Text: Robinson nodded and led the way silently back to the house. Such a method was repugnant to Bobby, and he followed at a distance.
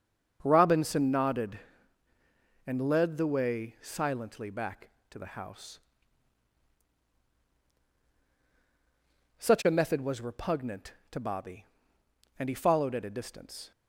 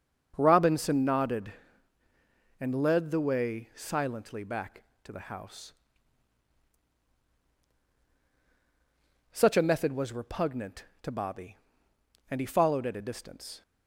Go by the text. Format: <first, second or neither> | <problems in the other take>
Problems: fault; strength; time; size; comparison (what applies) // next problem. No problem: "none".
neither | starts louder than the rest; the same in both